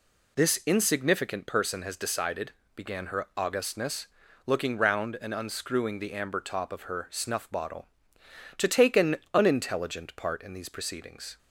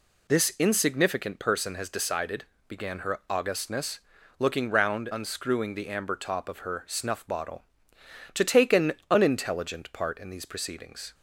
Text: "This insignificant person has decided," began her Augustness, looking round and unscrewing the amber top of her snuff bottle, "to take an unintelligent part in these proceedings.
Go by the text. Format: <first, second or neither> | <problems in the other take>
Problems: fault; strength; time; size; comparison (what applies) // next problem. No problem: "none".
first | skips "and"; at 5.1 s // pauses between "an" and "unintelligent"; slight; at 8.9 s; 0.18 s long; slight in the first